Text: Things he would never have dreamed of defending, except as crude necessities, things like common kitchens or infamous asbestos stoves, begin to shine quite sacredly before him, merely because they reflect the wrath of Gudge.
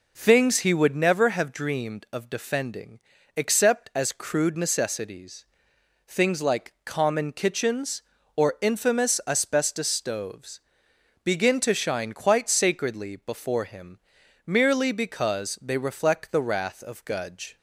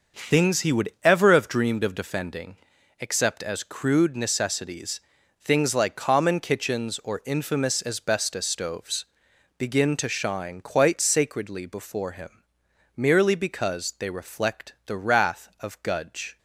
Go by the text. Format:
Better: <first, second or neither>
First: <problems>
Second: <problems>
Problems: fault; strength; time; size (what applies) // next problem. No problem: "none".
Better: first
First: none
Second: says "ever" for "never"; at 1.0 s